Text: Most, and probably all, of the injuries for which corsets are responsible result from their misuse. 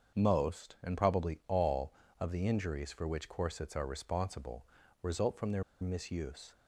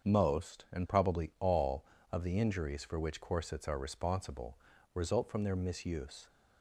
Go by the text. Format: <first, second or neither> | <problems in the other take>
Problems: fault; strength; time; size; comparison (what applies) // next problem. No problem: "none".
second | starts louder than the rest; until 1.2 s; 7 dB; also in the second // pauses between "responsible" and "result"; slight; at 4.6 s; 0.36 s long; slight in the second // pauses between "their" and "misuse"; slight; at 5.6 s; 0.17 s long